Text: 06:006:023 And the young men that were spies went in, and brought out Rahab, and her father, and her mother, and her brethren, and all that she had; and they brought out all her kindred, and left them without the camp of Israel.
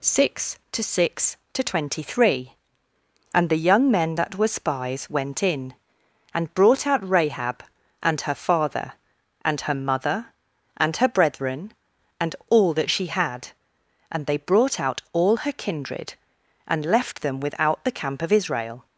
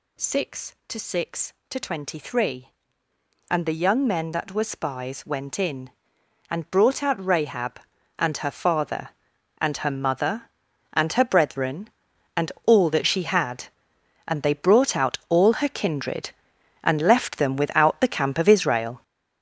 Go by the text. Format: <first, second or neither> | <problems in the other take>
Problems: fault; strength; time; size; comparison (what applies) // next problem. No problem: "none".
first | gets louder; strong; throughout; 9 dB